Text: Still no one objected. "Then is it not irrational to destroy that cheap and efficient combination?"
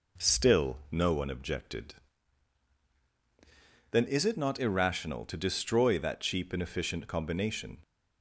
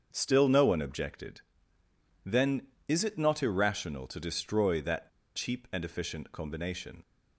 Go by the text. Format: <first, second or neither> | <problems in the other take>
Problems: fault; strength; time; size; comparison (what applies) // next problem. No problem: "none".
first | starts louder than the rest; until 1.1 s; 7 dB // pauses between "that" and "cheap"; slight; at 5.0 s; 0.27 s long